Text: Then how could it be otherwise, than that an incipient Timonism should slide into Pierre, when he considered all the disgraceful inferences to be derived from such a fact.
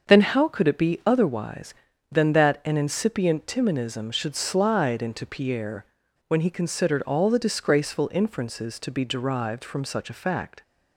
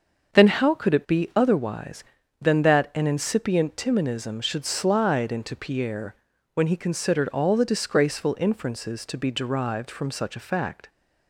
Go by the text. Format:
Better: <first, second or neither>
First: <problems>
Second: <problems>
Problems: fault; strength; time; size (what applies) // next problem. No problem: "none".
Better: neither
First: starts louder than the rest; until 1.1 s; 6.5 dB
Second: starts louder than the rest; until 1.4 s; 6.5 dB